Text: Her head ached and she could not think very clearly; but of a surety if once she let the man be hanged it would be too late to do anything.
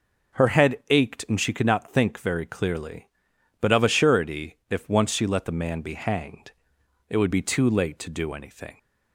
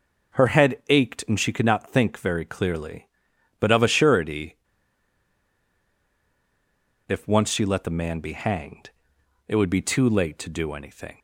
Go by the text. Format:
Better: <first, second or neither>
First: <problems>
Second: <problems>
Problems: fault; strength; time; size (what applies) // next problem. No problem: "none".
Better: first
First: pauses between "hanged" and "it"; noticeable; at 6.4 s; 0.58 s long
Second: pauses between "surety" and "if"; strong; at 4.5 s; 2.4 s long // pauses between "hanged" and "it"; noticeable; at 8.8 s; 0.58 s long